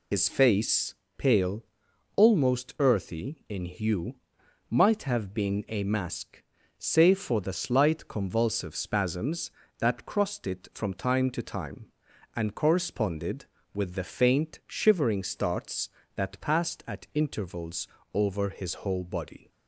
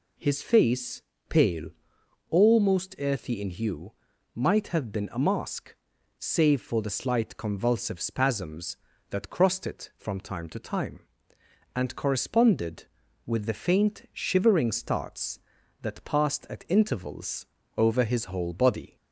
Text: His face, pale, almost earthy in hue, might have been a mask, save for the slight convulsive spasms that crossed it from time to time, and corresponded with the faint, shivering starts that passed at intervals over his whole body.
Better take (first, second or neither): second